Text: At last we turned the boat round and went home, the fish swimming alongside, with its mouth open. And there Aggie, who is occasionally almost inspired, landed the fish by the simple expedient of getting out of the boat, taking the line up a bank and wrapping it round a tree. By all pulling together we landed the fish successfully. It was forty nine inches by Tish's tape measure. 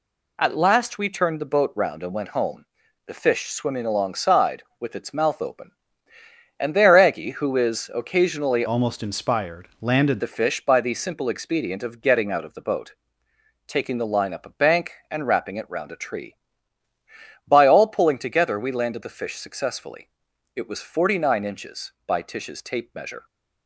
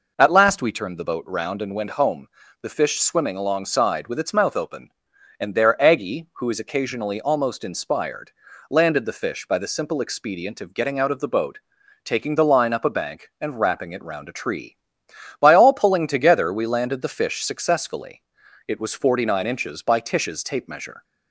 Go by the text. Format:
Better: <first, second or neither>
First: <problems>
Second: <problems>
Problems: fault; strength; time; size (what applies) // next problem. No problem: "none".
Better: second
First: changes voice from "almost" to "landed"; from 8.6 to 10.2 s; 1.6 s long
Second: none